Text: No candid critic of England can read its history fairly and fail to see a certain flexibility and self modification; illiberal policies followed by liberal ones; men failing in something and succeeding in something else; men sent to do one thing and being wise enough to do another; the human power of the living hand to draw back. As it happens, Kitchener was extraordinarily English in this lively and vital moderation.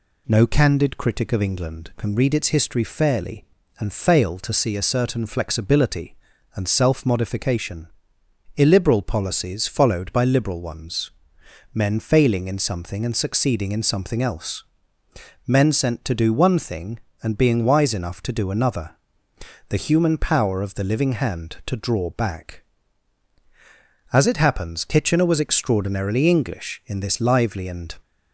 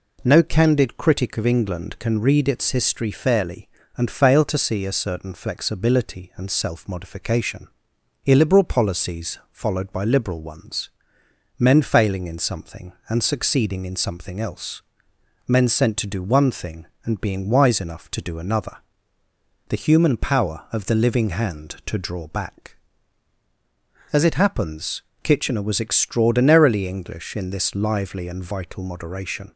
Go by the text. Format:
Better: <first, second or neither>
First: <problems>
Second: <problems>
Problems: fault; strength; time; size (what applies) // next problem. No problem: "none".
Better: second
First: stops before "vital moderation"; at 28.0 s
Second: none